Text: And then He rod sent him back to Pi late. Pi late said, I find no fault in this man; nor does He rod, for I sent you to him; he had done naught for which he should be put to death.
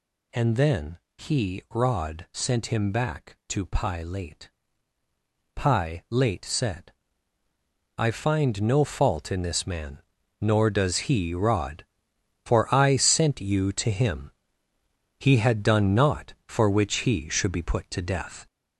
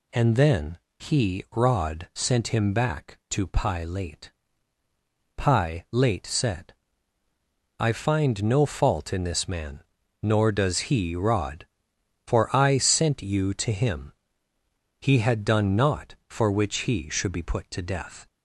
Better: second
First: gets louder; throughout; 3.5 dB // pauses between "then" and "He"; slight; at 0.9 s; 0.18 s long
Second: pauses between "then" and "He"; slight; at 0.7 s; 0.20 s long

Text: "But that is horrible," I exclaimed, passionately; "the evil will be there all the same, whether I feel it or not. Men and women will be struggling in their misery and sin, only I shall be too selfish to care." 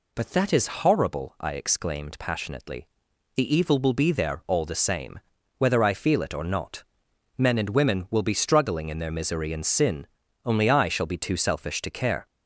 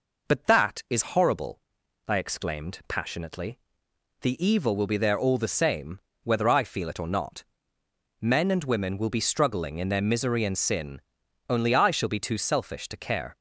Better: neither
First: none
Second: none

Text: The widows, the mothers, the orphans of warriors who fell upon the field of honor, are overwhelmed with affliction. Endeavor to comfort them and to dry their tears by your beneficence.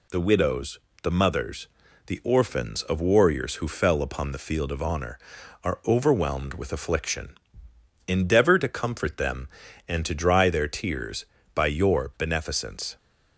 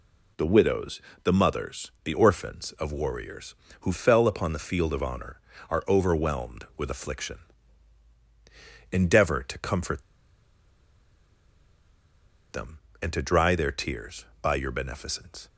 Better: first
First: none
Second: pauses between "comfort" and "them"; strong; at 10.0 s; 2.4 s long

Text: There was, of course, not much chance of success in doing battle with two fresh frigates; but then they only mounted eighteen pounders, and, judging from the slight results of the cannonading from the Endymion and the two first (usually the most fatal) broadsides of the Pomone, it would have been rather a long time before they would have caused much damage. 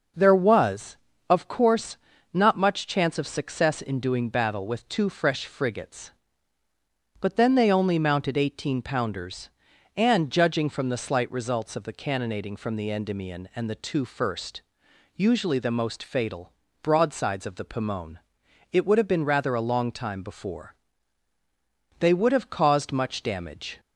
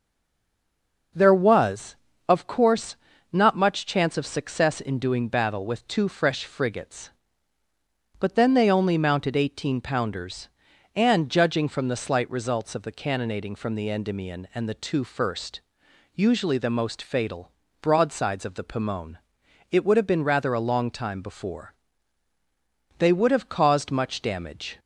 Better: first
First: starts louder than the rest; noticeable; until 1.4 s; 6 dB // pauses between "before" and "they"; at 20.7 s; 1.2 s long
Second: stays silent before the first word; until 1.1 s; 1.1 s long // starts louder than the rest; noticeable; until 2.4 s; 6 dB // pauses between "before" and "they"; at 21.7 s; 1.2 s long

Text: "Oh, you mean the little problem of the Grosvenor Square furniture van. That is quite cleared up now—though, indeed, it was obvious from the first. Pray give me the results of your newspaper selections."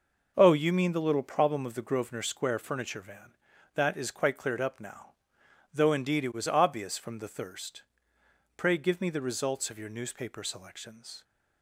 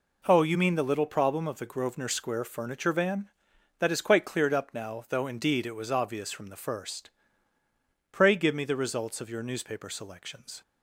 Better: second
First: says "thirst" for "first"; at 7.2 s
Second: none

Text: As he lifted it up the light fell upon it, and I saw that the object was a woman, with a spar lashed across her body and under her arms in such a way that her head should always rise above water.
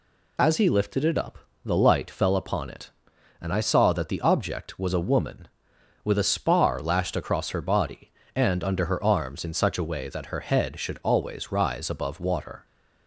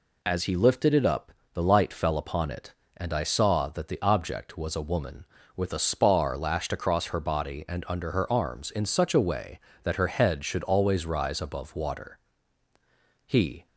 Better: first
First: pauses between "up" and "the"; slight; at 1.3 s; 0.28 s long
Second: pauses between "up" and "the"; slight; at 1.3 s; 0.22 s long // goes on to say "He"; slight; from 13.2 s on; 0.40 s long

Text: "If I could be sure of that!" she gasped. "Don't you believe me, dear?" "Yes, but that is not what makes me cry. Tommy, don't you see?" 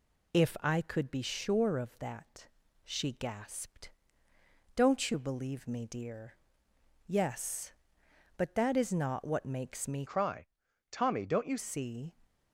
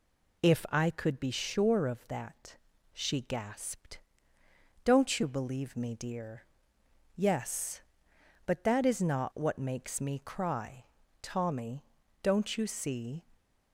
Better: second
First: changes voice from "cry" to "you"; from 10.0 to 11.5 s; 1.5 s long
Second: none

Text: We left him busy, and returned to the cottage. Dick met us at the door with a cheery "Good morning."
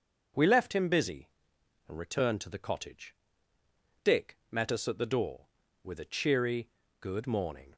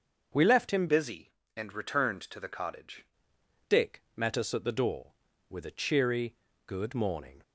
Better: first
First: starts louder than the rest; until 1.9 s; 6.5 dB // pauses between "cheery" and "Good"; slight; at 6.6 s; 0.32 s long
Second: starts louder than the rest; until 1.5 s; 6.5 dB // changes voice from "busy" to "cottage"; from 0.8 to 3.0 s; 2.2 s long // pauses between "cheery" and "Good"; slight; at 6.3 s; 0.32 s long

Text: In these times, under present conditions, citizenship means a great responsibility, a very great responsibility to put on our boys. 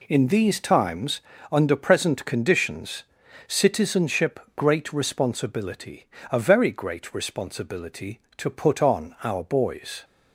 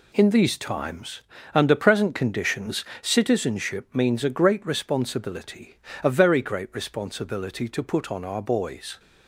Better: second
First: skips "means a"; at 4.4 s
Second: none

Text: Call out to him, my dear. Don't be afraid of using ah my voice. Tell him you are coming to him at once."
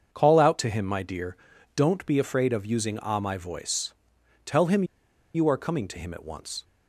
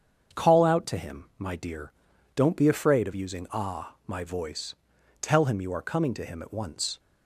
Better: second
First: starts louder than the rest; until 1.1 s; 6.5 dB // pauses between "him" and "you"; noticeable; at 4.8 s; 0.50 s long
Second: starts louder than the rest; strong; until 1.4 s; 7 dB

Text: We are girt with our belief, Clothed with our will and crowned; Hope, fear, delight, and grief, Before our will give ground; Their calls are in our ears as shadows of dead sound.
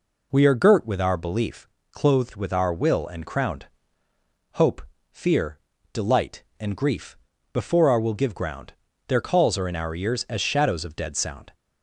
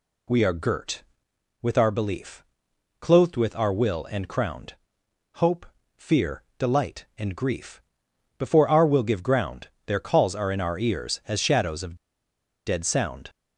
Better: first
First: none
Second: pauses between "of" and "dead"; noticeable; at 11.9 s; 0.71 s long

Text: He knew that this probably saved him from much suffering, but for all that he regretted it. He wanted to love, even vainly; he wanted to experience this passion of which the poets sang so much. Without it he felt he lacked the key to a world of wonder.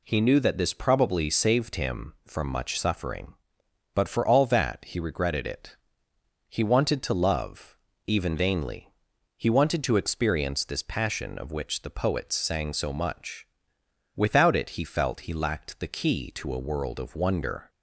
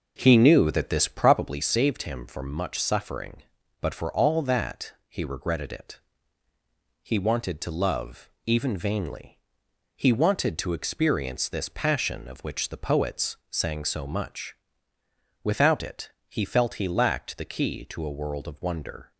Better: first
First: none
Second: starts louder than the rest; noticeable; until 1.6 s; 5.5 dB // pauses between "it" and "he"; slight; at 16.0 s; 0.18 s long

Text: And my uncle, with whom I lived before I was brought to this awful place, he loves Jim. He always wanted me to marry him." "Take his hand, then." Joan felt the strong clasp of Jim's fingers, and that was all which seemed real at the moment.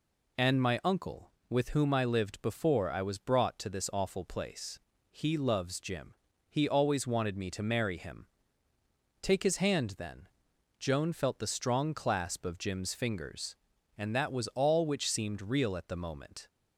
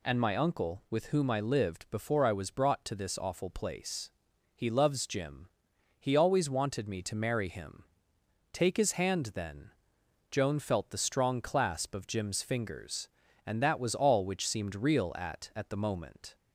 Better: first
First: none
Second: says "at" twice; at 15.5 s

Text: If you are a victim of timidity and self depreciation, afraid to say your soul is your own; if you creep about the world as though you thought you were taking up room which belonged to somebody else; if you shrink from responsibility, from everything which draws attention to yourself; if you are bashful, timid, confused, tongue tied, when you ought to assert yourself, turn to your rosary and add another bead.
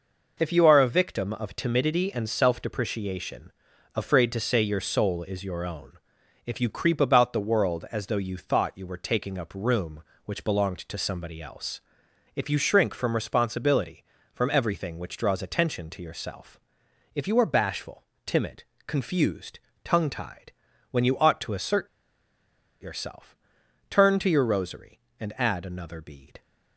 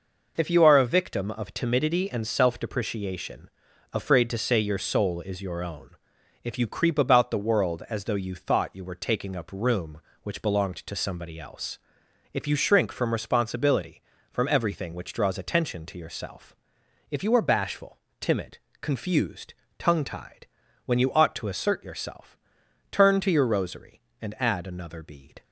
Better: second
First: pauses between "assert" and "yourself"; noticeable; at 21.8 s; 0.94 s long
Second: none

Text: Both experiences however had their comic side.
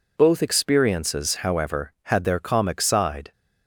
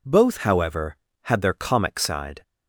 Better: first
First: none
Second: skips "experiences"; at 0.3 s

